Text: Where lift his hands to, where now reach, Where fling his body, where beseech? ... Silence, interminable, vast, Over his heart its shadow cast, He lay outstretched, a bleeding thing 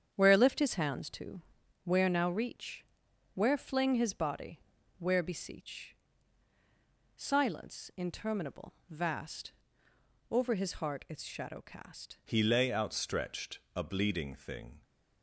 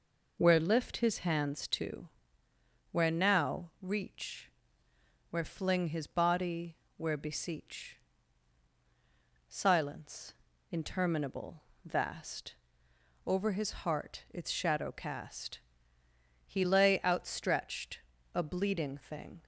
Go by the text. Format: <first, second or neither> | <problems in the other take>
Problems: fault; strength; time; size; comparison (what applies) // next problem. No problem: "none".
second | starts louder than the rest; strong; until 1.1 s; 8 dB // changes voice at "He"; from 12.2 s on; 2.6 s long